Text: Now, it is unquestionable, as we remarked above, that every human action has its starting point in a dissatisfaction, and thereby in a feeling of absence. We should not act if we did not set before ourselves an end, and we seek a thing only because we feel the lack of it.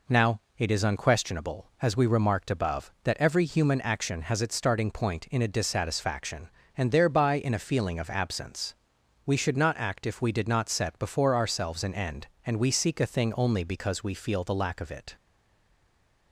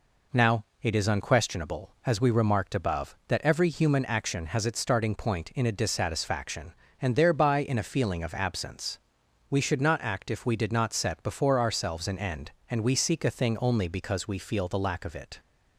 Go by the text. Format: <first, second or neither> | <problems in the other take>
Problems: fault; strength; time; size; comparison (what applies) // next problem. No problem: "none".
second | stays silent after the last word; from 15.1 s on; 1.2 s long